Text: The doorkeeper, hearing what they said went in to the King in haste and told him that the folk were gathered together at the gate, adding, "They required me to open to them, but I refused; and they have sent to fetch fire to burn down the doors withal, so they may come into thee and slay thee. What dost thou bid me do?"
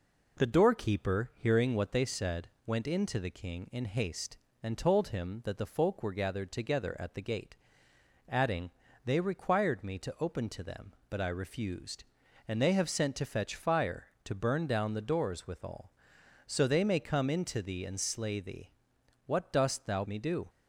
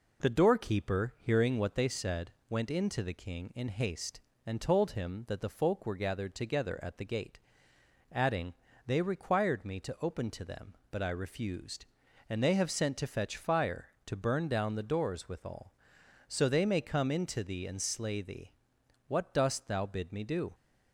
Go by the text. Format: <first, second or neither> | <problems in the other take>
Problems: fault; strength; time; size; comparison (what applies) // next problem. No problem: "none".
second | pauses between "said" and "went"; slight; at 2.4 s; 0.18 s long; slight in the second // skips "bid"; at 20.0 s